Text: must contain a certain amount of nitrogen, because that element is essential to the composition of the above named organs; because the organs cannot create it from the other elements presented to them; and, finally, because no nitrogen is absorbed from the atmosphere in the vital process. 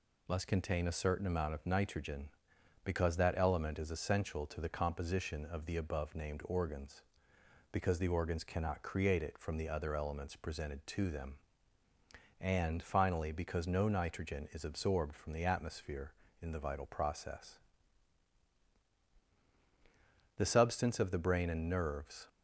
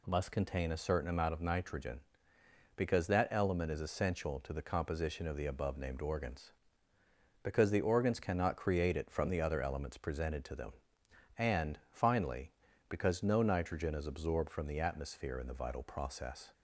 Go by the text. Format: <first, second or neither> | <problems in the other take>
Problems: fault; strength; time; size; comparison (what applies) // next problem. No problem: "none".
second | goes on to say "The substance of the brain and nerves"; strong; from 20.3 s on; 1.9 s long